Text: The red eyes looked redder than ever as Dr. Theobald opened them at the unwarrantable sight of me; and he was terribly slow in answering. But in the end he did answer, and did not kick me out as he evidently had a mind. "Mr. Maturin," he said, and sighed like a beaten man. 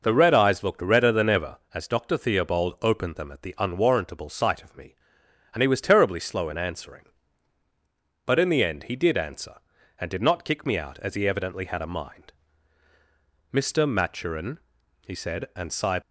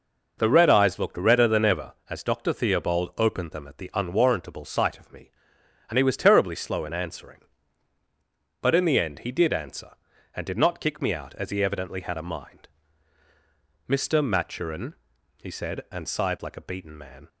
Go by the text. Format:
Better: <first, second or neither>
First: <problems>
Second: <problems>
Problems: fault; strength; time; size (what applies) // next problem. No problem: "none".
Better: second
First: stops before "like a beaten man"; at 16.0 s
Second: none